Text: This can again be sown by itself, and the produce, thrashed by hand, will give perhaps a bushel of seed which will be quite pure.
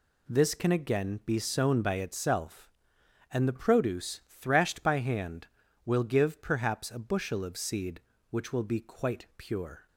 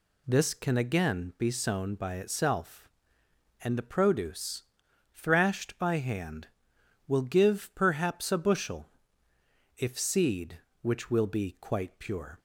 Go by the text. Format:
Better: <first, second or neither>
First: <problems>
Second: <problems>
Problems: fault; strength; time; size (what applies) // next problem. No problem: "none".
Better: first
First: none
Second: says "if" for "of"; at 9.7 s